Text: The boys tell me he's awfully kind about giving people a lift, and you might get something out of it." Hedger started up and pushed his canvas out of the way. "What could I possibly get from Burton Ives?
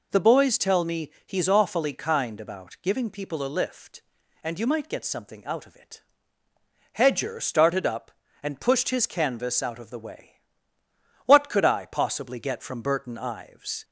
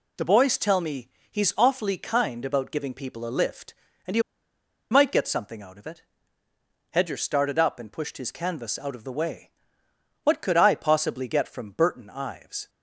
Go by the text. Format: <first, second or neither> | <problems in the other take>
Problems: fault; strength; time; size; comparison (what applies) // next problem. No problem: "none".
first | pauses between "me" and "he's"; slight; at 1.0 s; 0.22 s long // pauses between "you" and "might"; noticeable; at 4.2 s; 0.68 s long